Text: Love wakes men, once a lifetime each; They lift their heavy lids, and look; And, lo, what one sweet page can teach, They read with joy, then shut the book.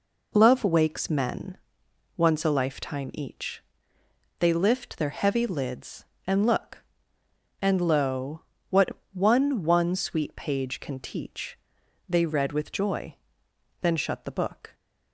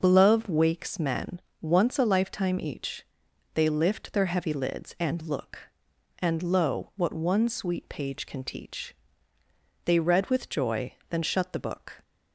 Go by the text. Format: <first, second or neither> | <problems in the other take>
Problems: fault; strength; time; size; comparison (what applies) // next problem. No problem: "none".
second | pauses between "what" and "one"; slight; at 8.8 s; 0.24 s long // says "one" twice; at 9.6 s